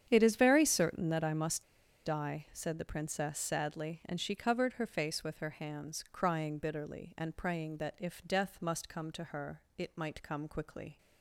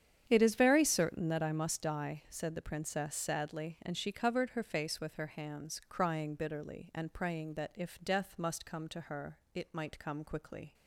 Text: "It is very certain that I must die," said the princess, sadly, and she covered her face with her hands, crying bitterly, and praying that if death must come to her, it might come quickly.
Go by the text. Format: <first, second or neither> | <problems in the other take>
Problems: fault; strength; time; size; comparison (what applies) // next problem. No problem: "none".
second | starts louder than the rest; strong; until 1.1 s; 8.5 dB; strong in the second // pauses between "must" and "die"; at 1.6 s; 0.42 s long